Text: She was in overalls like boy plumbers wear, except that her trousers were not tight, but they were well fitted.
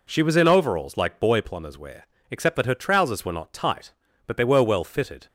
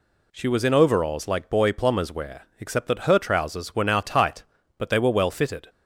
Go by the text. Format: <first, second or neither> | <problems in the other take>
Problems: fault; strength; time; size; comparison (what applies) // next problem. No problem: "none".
first | says "now" for "not"; at 3.8 s